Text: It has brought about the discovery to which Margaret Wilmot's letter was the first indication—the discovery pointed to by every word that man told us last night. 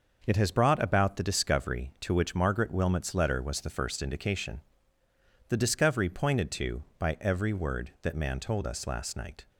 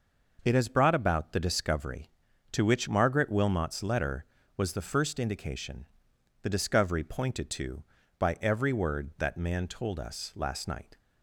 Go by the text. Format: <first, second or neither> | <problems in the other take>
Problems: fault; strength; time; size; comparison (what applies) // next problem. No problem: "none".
neither | none